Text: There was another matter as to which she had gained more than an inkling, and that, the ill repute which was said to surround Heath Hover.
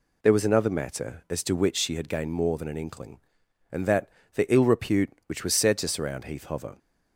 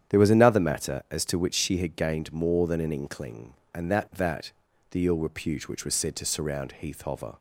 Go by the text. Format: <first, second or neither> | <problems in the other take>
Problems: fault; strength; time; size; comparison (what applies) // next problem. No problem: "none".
first | starts louder than the rest; strong; until 1.1 s; 9 dB // says "that" twice; at 4.1 s